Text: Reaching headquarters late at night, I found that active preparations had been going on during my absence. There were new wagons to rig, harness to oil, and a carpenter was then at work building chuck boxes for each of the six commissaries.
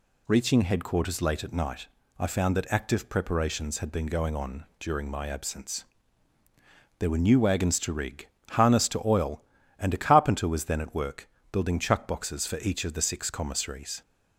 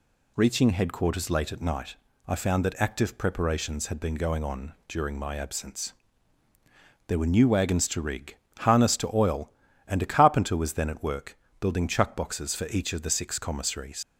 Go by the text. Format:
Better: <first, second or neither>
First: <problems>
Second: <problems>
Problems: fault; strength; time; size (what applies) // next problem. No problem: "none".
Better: first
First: pauses between "work" and "building"; slight; at 11.2 s; 0.24 s long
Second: pauses between "work" and "building"; slight; at 11.3 s; 0.24 s long // leaves "commissaries" unfinished; at 14.0 s; 70 ms